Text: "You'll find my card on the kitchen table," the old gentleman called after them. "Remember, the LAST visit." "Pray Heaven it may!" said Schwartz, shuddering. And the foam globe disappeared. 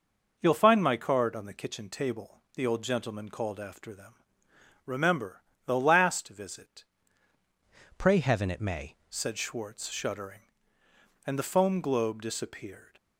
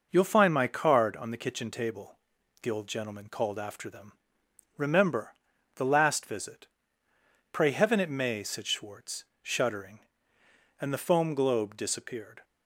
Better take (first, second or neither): second